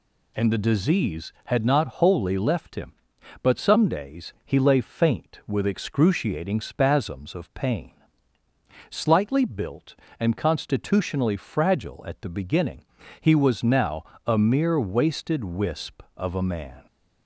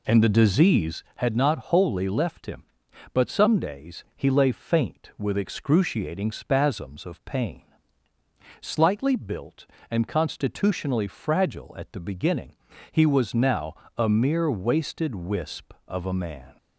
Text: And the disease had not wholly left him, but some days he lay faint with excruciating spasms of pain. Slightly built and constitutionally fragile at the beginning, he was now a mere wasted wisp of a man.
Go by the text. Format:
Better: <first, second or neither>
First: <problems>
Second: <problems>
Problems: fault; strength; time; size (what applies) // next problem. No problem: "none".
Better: first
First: pauses between "now" and "a"; slight; at 14.0 s; 0.22 s long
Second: starts louder than the rest; slight; until 1.1 s; 2.5 dB // pauses between "now" and "a"; slight; at 13.7 s; 0.22 s long